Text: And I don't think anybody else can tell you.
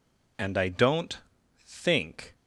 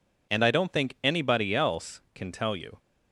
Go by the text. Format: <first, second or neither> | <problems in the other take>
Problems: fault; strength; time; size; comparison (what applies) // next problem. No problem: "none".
second | pauses between "don't" and "think"; noticeable; at 1.1 s; 0.48 s long // stops before "anybody else can tell you"; at 2.3 s